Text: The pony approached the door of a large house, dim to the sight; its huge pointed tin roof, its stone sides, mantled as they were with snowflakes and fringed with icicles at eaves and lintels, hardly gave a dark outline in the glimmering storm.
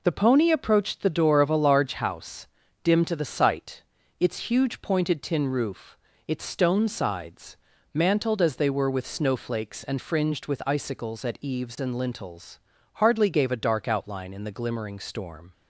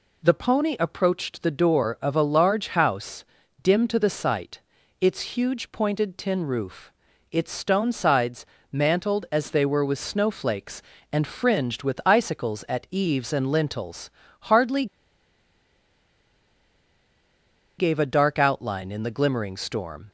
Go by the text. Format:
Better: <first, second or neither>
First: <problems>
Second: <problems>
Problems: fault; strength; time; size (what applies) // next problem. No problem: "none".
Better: first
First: none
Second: pauses between "hardly" and "gave"; strong; at 14.8 s; 2.9 s long